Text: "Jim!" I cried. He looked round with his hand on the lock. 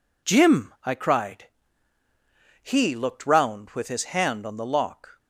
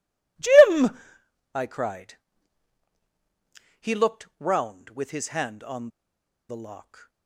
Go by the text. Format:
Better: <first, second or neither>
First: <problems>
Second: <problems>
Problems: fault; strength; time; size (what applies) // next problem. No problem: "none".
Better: first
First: none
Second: pauses between "on" and "the"; noticeable; at 5.8 s; 0.61 s long